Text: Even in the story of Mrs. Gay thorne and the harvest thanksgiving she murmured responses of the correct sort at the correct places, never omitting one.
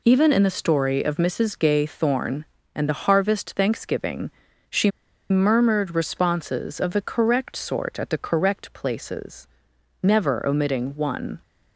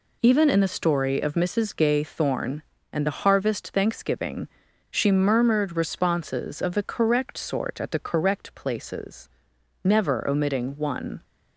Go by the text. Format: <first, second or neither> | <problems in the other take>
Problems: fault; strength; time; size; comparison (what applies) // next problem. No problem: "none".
second | pauses between "thanksgiving" and "she"; slight; at 4.3 s; 0.36 s long; also in the second // pauses between "she" and "murmured"; at 4.9 s; 0.39 s long